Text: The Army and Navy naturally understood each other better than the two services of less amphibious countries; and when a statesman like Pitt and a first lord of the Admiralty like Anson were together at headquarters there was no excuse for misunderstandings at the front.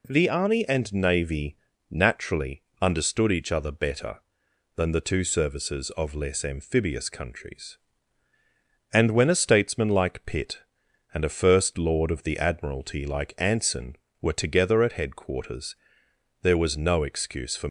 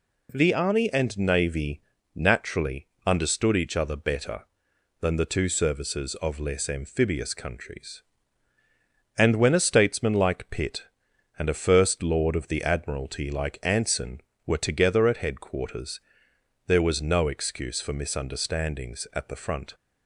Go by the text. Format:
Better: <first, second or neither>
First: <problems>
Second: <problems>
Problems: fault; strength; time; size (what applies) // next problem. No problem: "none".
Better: second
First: pauses between "Navy" and "naturally"; slight; at 1.5 s; 0.34 s long // pauses between "naturally" and "understood"; slight; at 2.6 s; 0.18 s long // pauses between "headquarters" and "there"; noticeable; at 15.7 s; 0.70 s long // stops before "misunderstandings at the front"; at 17.6 s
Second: pauses between "Navy" and "naturally"; slight; at 1.8 s; 0.34 s long // pauses between "naturally" and "understood"; slight; at 2.8 s; 0.18 s long // pauses between "headquarters" and "there"; noticeable; at 15.9 s; 0.70 s long